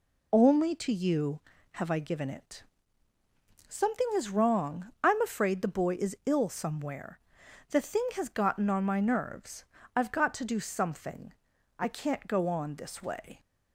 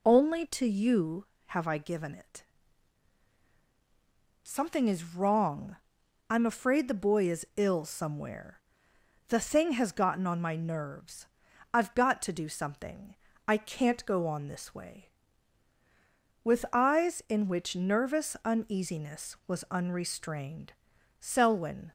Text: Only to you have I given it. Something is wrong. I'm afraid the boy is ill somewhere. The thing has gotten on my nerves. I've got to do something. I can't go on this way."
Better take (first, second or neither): first